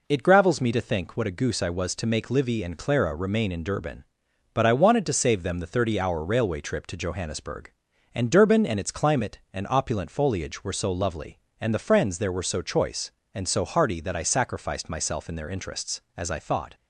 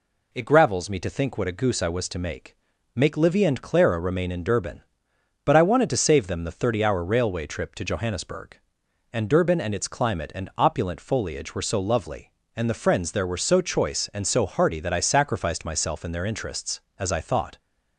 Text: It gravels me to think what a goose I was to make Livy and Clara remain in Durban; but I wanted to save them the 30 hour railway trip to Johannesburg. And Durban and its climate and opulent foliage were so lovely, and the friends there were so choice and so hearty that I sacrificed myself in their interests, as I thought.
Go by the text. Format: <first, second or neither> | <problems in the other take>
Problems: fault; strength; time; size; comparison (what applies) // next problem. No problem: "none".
first | says "make" twice; at 2.9 s